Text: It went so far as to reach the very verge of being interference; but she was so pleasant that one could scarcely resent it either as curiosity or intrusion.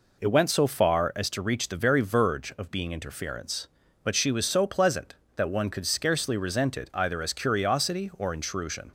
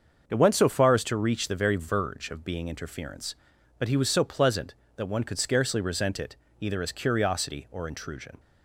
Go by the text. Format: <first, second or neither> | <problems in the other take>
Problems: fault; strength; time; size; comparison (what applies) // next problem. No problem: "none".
first | starts louder than the rest; until 1.2 s; 6.5 dB // says "he" for "she"; at 3.8 s // pauses between "it" and "either"; slight; at 6.3 s; 0.24 s long